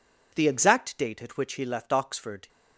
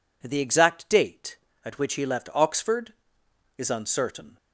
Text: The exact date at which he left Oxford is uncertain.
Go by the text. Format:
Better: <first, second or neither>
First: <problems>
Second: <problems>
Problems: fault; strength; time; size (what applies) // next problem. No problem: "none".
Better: second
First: stops before "is uncertain"; at 2.4 s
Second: none